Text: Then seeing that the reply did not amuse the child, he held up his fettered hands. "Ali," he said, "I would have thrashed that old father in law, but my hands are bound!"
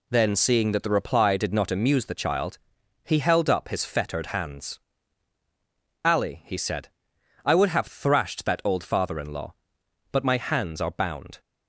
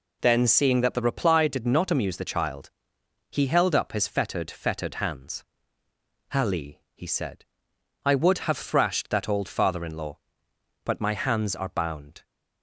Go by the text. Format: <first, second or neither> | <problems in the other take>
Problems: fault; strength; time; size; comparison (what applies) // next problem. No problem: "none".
first | says "fettered" twice; at 4.4 s